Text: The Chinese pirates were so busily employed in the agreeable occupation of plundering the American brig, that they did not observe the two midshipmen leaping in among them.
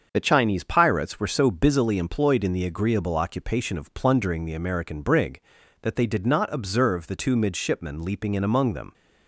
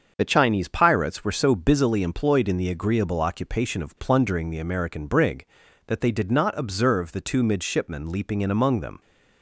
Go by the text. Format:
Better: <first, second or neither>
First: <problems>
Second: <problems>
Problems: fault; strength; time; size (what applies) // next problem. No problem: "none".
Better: neither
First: starts louder than the rest; until 1.1 s; 6.5 dB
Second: starts louder than the rest; until 1.1 s; 7 dB